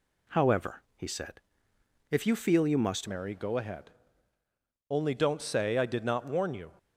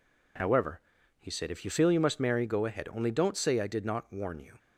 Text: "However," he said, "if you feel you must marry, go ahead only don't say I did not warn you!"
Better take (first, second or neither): second